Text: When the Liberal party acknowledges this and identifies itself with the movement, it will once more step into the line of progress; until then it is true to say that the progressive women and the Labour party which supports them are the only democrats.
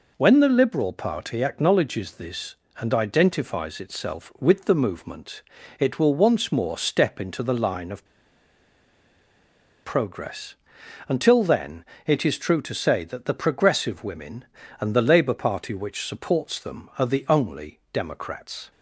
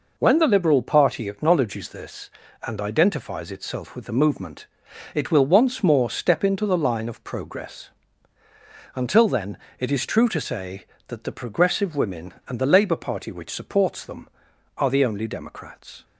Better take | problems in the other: second | pauses between "of" and "progress"; strong; at 8.0 s; 1.7 s long // pauses between "then" and "it"; slight; at 11.8 s; 0.22 s long; slight in the second

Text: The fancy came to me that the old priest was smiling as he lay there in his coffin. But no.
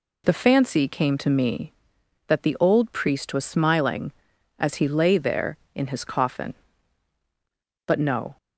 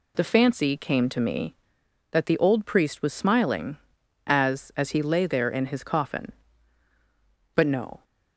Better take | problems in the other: first | says "as" twice; at 4.7 s

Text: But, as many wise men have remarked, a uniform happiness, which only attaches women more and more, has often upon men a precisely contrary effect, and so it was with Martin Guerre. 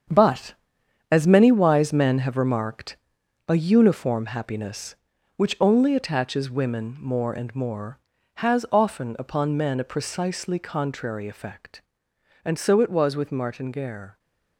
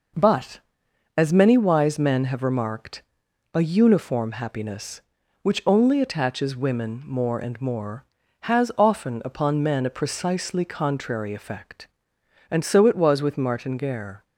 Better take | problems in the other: second | gets quieter; strong; throughout; 9.5 dB

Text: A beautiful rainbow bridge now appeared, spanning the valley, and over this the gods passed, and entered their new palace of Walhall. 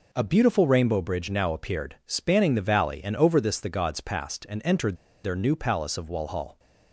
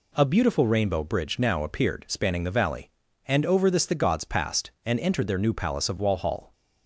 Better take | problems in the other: second | pauses between "entered" and "their"; slight; at 4.9 s; 0.28 s long

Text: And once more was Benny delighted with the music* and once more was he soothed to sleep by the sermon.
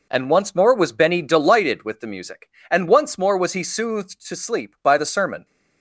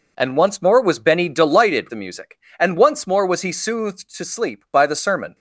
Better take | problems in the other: first | skips "with"; at 1.8 s

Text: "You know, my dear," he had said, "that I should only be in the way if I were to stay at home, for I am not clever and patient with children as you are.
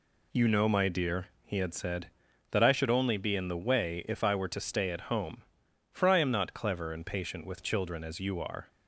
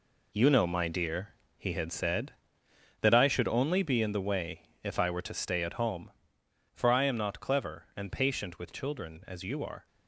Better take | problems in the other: first | gets quieter; strong; throughout; 9 dB // pauses between "way" and "if"; slight; at 4.6 s; 0.16 s long

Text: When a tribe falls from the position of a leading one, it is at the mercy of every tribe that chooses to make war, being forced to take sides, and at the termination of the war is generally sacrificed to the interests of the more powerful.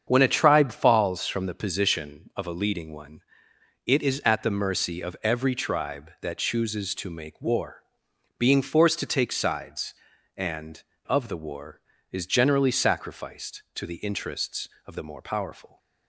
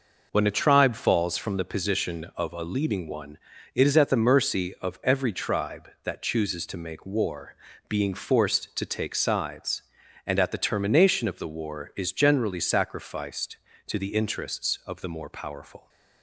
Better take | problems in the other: second | starts louder than the rest; strong; until 1.0 s; 7.5 dB // skips "at the termination"; at 10.9 s

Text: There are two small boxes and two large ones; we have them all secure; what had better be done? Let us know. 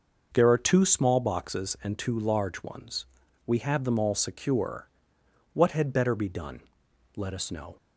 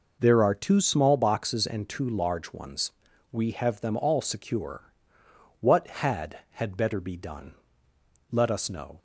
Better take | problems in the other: first | says "had" twice; at 6.5 s

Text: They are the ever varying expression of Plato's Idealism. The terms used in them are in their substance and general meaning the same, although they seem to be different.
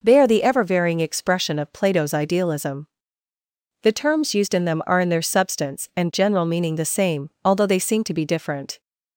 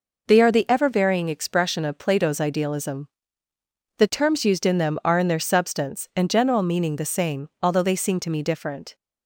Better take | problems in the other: first | says "me" for "be"; at 8.3 s

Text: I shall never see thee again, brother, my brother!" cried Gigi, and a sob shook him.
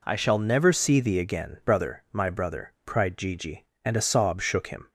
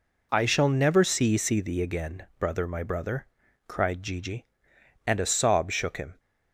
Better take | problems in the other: first | says "see" twice; at 1.3 s

